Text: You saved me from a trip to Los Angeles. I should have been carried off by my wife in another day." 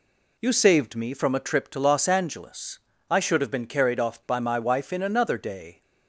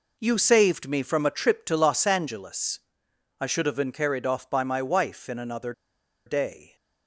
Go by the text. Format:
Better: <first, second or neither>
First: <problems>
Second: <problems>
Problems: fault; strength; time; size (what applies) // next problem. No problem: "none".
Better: first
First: none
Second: pauses between "another" and "day"; noticeable; at 5.7 s; 0.54 s long